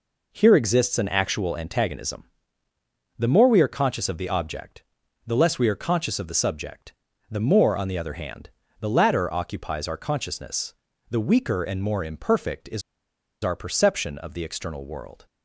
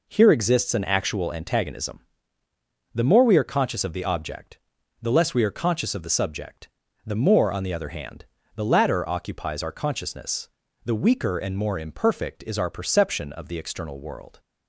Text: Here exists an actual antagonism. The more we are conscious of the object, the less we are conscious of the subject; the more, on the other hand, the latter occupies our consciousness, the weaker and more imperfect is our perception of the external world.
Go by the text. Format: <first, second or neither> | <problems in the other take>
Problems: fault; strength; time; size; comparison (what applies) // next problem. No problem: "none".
second | pauses between "is" and "our"; noticeable; at 12.8 s; 0.62 s long